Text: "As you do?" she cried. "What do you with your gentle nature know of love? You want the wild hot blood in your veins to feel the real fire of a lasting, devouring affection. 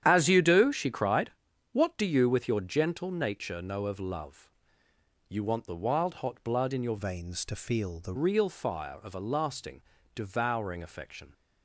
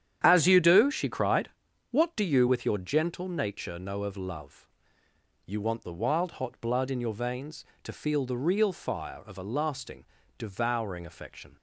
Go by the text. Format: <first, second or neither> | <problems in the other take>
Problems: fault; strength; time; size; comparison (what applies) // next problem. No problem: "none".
second | starts louder than the rest; strong; until 1.0 s; 10 dB; strong in the second // changes voice from "veins" to "the"; from 6.9 to 8.1 s; 1.2 s long